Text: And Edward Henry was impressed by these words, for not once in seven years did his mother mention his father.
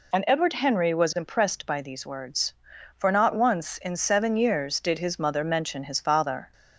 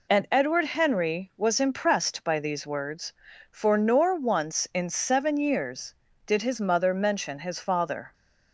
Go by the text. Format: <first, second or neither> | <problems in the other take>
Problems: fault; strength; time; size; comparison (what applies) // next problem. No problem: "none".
first | says "nor" for "not"; at 3.7 s